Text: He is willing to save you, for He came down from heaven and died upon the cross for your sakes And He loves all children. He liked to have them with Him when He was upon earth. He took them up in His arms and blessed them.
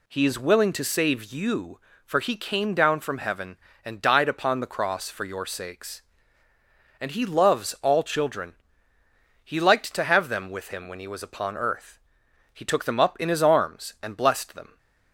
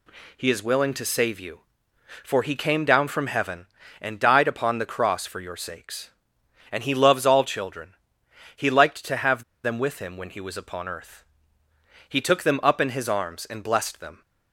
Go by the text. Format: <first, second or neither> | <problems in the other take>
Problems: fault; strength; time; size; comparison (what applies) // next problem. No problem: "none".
first | pauses between "have" and "them"; slight; at 9.4 s; 0.22 s long